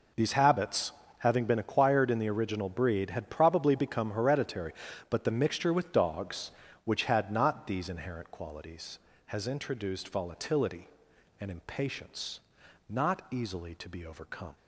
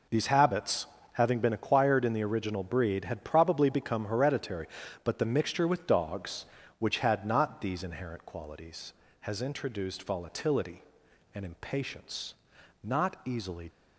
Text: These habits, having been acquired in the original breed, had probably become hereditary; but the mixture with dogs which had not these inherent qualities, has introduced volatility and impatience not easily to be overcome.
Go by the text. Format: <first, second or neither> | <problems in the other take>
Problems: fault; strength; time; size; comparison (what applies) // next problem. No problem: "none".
first | pauses between "impatience" and "not"; noticeable; at 12.3 s; 0.50 s long; noticeable in the first // stops before "to be overcome"; at 13.6 s